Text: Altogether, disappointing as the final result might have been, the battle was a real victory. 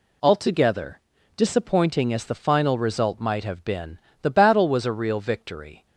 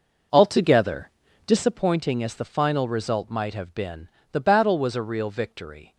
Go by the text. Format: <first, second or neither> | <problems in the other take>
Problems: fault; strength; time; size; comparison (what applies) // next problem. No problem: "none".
first | starts louder than the rest; noticeable; until 1.8 s; 5.5 dB